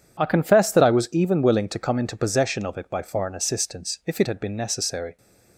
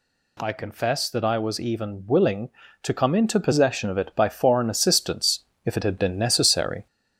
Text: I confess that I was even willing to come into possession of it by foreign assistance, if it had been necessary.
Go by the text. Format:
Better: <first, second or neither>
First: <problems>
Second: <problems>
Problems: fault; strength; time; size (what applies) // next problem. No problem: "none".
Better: first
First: none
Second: gets louder; slight; throughout; 2 dB